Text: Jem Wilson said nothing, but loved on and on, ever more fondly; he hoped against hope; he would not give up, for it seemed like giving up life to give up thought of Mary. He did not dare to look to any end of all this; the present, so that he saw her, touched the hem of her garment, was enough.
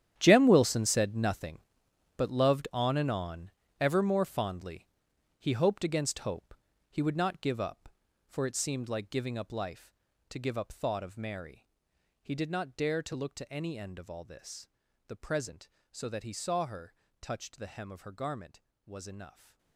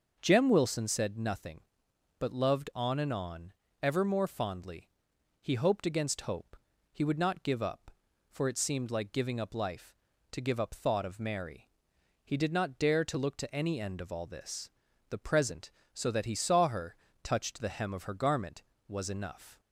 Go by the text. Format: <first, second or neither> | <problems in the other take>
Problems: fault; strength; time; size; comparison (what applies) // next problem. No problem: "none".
second | gets quieter; strong; throughout; 15.5 dB // starts louder than the rest; strong; until 1.1 s; 10.5 dB; also in the second